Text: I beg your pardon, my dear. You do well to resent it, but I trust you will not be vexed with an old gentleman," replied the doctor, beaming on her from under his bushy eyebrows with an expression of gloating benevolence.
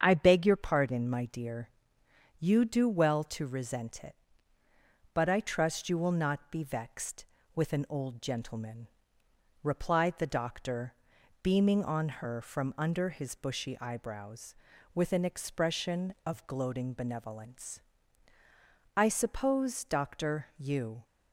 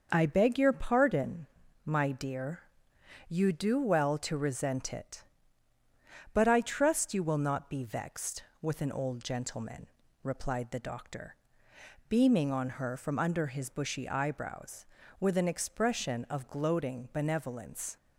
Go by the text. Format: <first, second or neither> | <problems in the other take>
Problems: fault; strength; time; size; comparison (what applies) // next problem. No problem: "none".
second | starts louder than the rest; strong; until 1.0 s; 7.5 dB; also in the second // goes on to say "I suppose doctor you"; strong; from 18.9 s on; 2.0 s long